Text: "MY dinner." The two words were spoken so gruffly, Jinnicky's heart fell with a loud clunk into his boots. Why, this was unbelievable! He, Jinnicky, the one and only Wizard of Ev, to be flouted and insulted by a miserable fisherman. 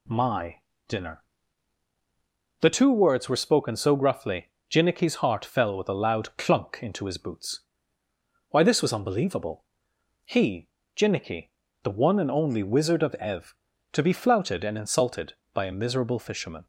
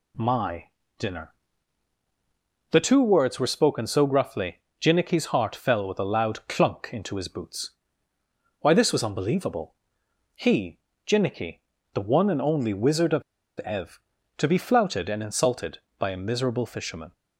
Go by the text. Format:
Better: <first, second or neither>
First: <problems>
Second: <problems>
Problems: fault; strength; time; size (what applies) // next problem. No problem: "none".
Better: first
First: pauses between "MY" and "dinner"; slight; at 0.6 s; 0.26 s long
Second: pauses between "MY" and "dinner"; slight; at 0.6 s; 0.28 s long // pauses between "of" and "Ev"; at 13.2 s; 0.37 s long